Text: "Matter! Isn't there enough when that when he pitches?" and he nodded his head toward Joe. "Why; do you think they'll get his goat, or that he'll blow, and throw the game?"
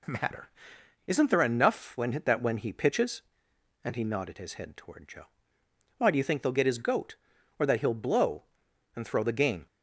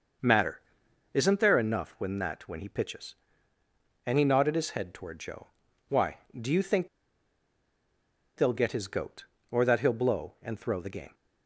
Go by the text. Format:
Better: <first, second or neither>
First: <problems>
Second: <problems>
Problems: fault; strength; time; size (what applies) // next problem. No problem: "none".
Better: first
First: none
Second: starts louder than the rest; noticeable; until 1.7 s; 6 dB // pauses between "think" and "they'll"; strong; at 6.8 s; 1.4 s long